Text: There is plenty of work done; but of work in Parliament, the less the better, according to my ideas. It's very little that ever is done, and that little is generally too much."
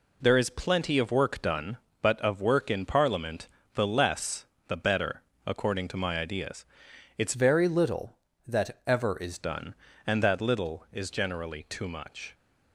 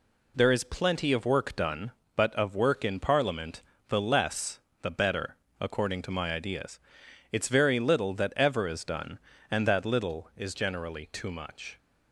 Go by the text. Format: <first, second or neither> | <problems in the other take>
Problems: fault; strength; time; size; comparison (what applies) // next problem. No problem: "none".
second | pauses between "less" and "the"; slight; at 4.4 s; 0.22 s long; slight in the second // changes voice from "very" to "is"; from 7.3 to 9.3 s; 2.0 s long